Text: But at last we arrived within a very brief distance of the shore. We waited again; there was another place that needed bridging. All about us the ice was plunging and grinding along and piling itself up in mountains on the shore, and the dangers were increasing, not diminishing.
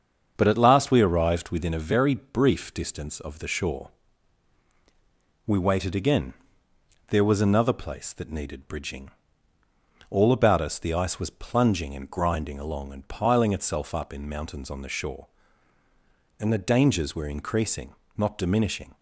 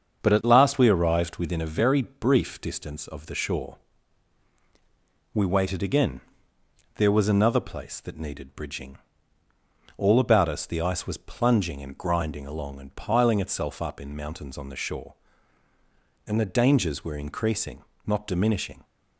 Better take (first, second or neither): neither